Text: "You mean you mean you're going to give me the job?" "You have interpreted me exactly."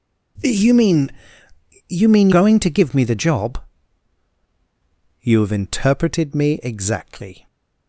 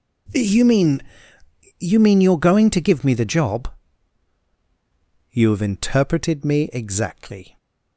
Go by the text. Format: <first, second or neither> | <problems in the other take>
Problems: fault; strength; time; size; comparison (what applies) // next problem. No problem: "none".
second | pauses between "mean" and "you"; noticeable; at 1.1 s; 0.78 s long; noticeable in the second // skips "you're"; at 2.3 s